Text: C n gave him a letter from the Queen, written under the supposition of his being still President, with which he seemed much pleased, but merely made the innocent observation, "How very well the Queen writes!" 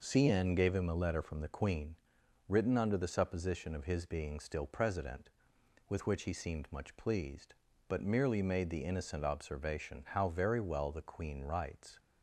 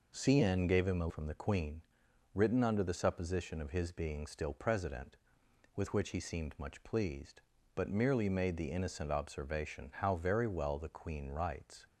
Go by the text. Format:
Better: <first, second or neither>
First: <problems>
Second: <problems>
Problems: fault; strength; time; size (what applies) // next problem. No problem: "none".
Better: first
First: none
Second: skips "letter"; at 1.0 s